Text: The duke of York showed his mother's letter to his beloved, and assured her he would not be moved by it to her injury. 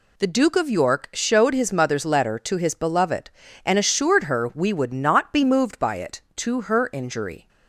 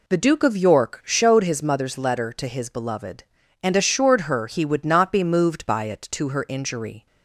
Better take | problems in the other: second | says "we" for "he"; at 4.5 s

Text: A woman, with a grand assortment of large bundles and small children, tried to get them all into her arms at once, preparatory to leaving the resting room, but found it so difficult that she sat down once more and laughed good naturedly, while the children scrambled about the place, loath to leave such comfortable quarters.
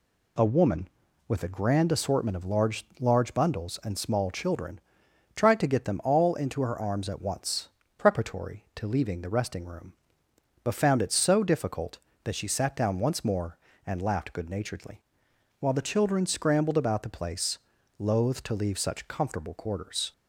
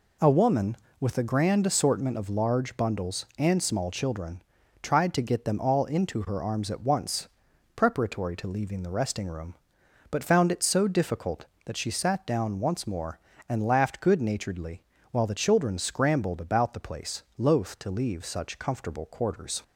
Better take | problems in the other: second | says "large" twice; at 2.9 s

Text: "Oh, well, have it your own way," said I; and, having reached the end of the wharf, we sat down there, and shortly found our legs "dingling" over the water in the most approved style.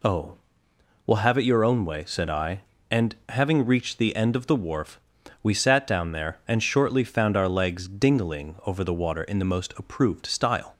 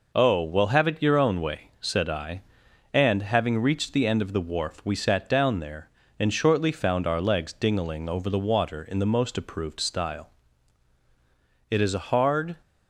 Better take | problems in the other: first | goes on to say "It is a hard"; noticeable; from 11.6 s on; 0.86 s long

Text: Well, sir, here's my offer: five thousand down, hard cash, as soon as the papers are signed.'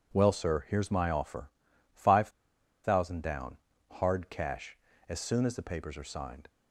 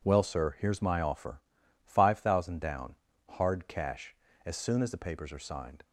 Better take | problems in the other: second | pauses between "five" and "thousand"; noticeable; at 2.2 s; 0.55 s long

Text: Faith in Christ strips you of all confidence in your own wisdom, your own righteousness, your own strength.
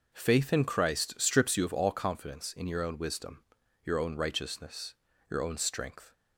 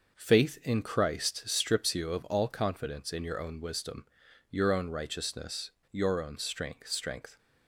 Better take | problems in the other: first | says "strength" twice; at 6.8 s

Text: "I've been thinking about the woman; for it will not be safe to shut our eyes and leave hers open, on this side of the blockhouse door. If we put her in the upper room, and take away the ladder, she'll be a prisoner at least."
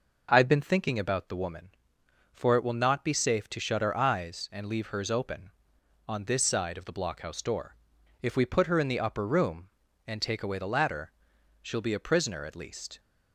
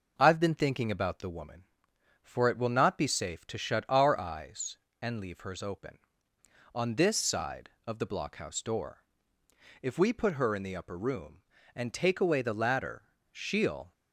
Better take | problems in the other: first | stops before "be a prisoner at least"; at 13.9 s

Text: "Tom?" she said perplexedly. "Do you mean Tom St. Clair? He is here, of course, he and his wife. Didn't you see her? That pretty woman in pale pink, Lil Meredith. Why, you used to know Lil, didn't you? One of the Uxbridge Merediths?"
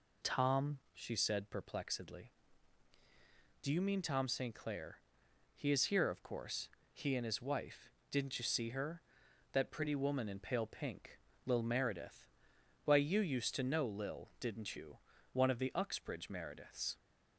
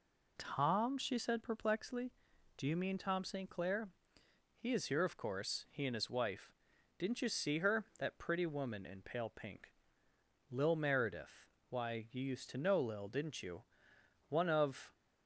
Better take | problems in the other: first | stops before "the Uxbridge Merediths"; at 14.9 s

